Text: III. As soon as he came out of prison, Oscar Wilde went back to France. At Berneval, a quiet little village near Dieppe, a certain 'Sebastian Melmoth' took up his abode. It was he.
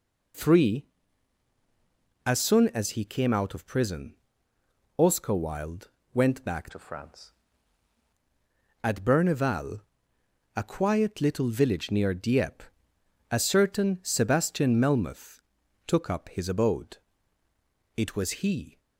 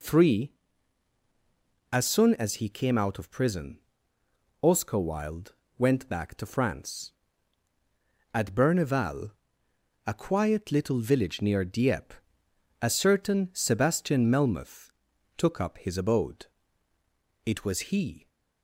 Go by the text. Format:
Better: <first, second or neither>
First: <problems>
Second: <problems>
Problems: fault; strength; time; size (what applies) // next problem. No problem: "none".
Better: second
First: pauses between "Wilde" and "went"; slight; at 5.8 s; 0.26 s long // changes voice from "to" to "France"; from 6.7 to 7.3 s; 0.6 s long // pauses between "Melmoth" and "took"; noticeable; at 15.3 s; 0.46 s long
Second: pauses between "Wilde" and "went"; slight; at 5.5 s; 0.26 s long // pauses between "Melmoth" and "took"; noticeable; at 14.8 s; 0.46 s long